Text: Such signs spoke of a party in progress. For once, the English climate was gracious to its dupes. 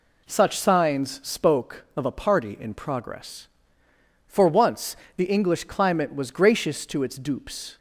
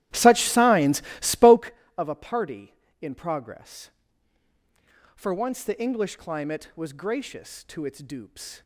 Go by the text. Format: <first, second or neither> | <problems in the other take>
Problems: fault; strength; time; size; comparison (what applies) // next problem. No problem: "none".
first | starts louder than the rest; strong; until 1.7 s; 14 dB // pauses between "signs" and "spoke"; slight; at 1.0 s; 0.18 s long